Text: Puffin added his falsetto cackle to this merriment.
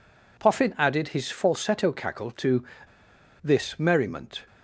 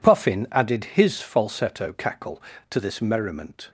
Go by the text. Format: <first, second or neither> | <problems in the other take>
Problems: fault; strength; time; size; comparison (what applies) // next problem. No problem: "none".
second | pauses between "to" and "this"; noticeable; at 2.6 s; 0.79 s long